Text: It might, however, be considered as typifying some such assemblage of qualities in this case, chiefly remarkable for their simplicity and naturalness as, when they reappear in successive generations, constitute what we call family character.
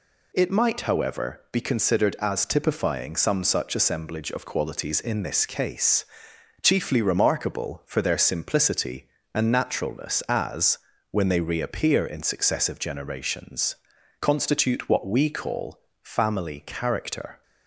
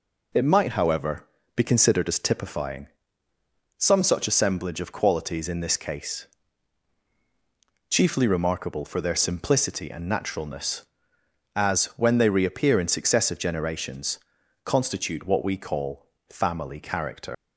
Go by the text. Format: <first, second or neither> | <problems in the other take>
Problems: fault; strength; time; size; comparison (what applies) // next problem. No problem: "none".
first | pauses between "typifying" and "some"; noticeable; at 2.8 s; 0.90 s long // pauses between "call" and "family"; slight; at 16.0 s; 0.22 s long; slight in the first // leaves "character" unfinished; at 17.3 s; 115 ms